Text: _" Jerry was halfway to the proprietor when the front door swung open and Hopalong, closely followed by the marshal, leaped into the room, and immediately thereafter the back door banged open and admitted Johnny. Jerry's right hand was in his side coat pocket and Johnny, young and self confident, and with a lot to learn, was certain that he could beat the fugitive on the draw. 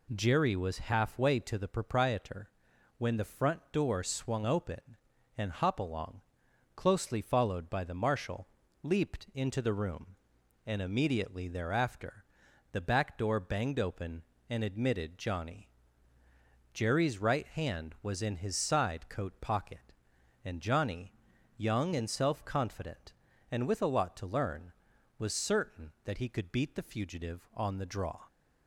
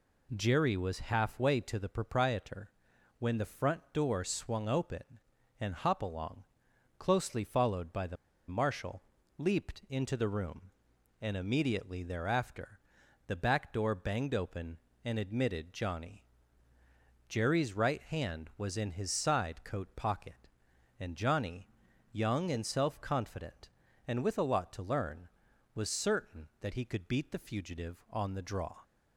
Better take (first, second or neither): first